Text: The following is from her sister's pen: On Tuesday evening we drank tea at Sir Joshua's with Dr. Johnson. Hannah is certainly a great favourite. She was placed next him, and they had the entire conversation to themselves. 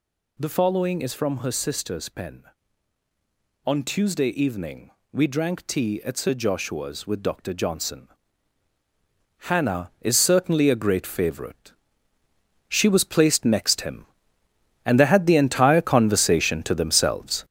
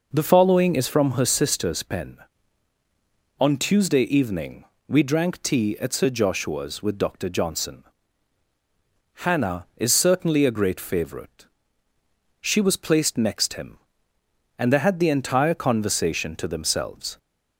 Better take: second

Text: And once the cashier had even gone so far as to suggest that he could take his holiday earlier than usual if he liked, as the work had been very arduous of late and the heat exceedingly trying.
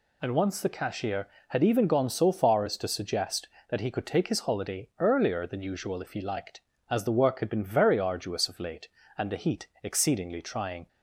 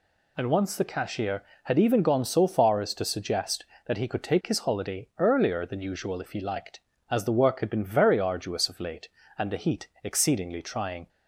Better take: neither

